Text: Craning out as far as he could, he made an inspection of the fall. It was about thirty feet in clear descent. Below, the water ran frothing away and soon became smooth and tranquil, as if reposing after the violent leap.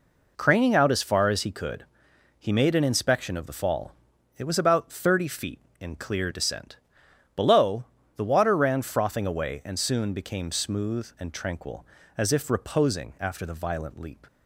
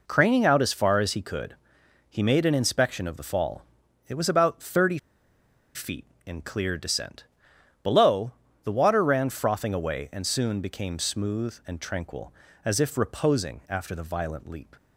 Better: first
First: none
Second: pauses between "thirty" and "feet"; noticeable; at 4.9 s; 0.77 s long

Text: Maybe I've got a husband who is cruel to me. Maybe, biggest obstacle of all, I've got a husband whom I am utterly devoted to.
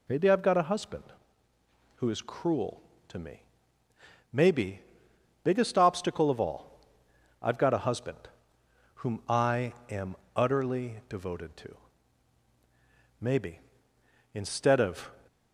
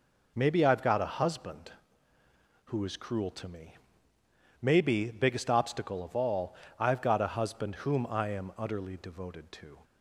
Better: second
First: pauses between "husband" and "whom"; noticeable; at 8.1 s; 0.78 s long // pauses between "I" and "am"; slight; at 9.7 s; 0.18 s long // pauses between "am" and "utterly"; slight; at 10.1 s; 0.18 s long // goes on to say "Maybe instead of"; strong; from 13.2 s on; 1.9 s long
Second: none

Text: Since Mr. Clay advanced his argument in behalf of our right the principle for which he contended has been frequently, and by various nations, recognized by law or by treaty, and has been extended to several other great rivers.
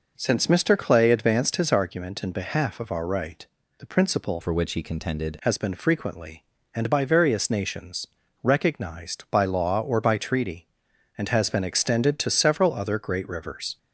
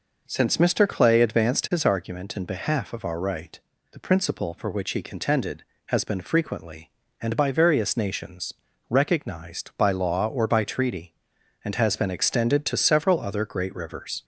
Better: second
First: pauses between "right" and "the"; slight; at 3.4 s; 0.34 s long // changes voice from "for" to "contended"; from 4.4 to 5.3 s; 0.9 s long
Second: pauses between "right" and "the"; slight; at 3.5 s; 0.34 s long

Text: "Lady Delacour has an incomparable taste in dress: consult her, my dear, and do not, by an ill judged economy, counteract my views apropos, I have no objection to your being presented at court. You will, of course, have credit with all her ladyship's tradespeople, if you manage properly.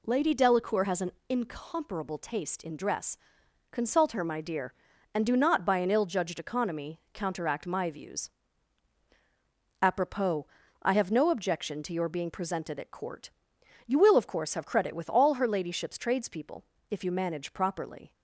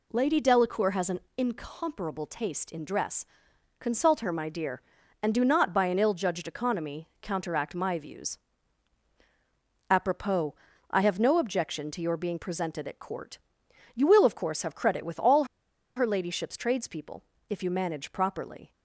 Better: first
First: pauses between "an" and "incomparable"; slight; at 1.1 s; 0.18 s long // pauses between "views" and "apropos"; strong; at 8.3 s; 1.5 s long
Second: pauses between "an" and "incomparable"; slight; at 1.1 s; 0.18 s long // pauses between "views" and "apropos"; strong; at 8.3 s; 1.5 s long // pauses between "all" and "her"; noticeable; at 15.4 s; 0.51 s long

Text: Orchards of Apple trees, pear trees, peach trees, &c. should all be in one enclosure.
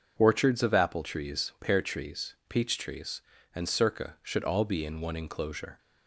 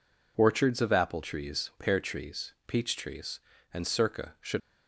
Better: first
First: none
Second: stops before "all be in one enclosure"; at 4.6 s

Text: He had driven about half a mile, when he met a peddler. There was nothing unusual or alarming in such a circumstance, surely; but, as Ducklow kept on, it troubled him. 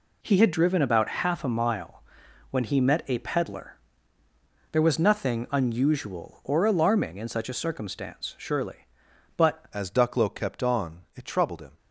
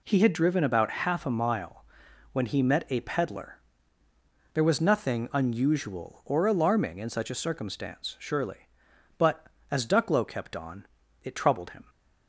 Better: second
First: changes voice at "as"; from 9.7 s on; 2.0 s long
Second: none

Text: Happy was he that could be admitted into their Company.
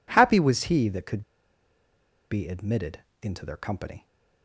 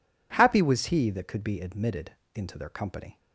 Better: second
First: pauses between "could" and "be"; at 1.2 s; 1.1 s long // pauses between "admitted" and "into"; slight; at 2.9 s; 0.24 s long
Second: pauses between "admitted" and "into"; slight; at 2.1 s; 0.24 s long

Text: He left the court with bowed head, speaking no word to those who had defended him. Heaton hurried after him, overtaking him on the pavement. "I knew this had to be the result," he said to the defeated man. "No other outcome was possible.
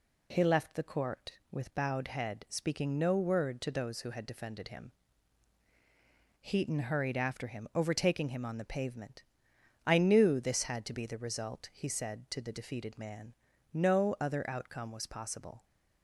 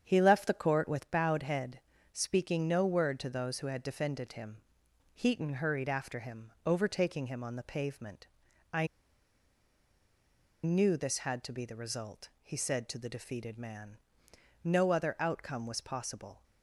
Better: first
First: none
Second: starts louder than the rest; strong; until 1.0 s; 8 dB // pauses between "I" and "knew"; strong; at 8.8 s; 1.7 s long

